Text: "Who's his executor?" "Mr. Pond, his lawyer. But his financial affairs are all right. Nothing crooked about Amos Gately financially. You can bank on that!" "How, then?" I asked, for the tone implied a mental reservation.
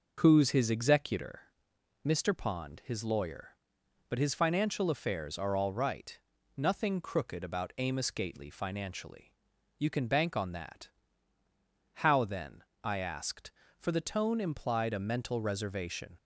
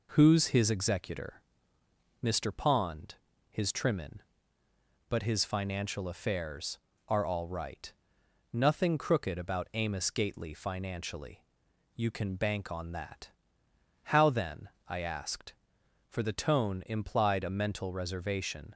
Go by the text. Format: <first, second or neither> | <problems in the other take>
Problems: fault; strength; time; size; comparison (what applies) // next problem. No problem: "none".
first | says "trimmin" for "lawyer"; at 3.6 s